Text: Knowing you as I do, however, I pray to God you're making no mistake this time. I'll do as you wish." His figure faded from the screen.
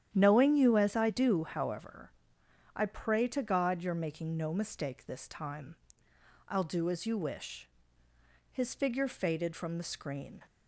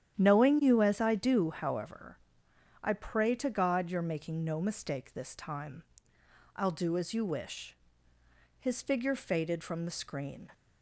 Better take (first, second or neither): neither